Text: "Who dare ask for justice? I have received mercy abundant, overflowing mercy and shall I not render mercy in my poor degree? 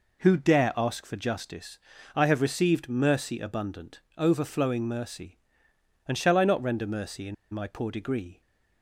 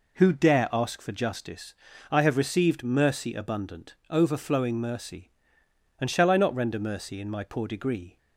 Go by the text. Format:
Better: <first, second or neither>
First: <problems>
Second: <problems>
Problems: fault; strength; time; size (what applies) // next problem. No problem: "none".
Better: second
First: pauses between "in" and "my"; slight; at 7.3 s; 0.17 s long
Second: none